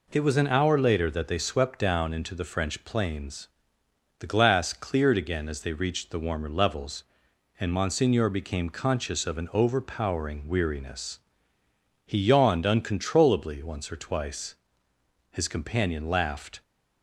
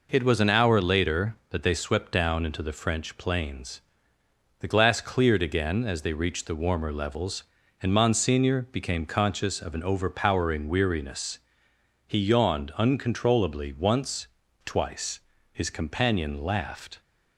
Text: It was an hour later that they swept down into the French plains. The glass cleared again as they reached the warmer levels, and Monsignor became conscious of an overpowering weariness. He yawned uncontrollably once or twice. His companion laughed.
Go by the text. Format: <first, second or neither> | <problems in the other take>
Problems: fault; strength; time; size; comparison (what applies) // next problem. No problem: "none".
first | skips "or"; at 14.4 s